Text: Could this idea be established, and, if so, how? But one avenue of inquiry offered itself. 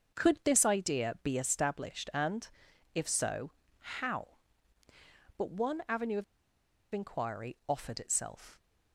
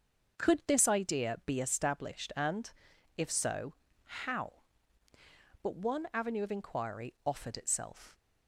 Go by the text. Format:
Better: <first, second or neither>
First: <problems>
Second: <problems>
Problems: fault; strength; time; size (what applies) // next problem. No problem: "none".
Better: second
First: starts louder than the rest; until 1.2 s; 6.5 dB // pauses between "of" and "inquiry"; noticeable; at 6.2 s; 0.69 s long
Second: starts louder than the rest; until 1.5 s; 6.5 dB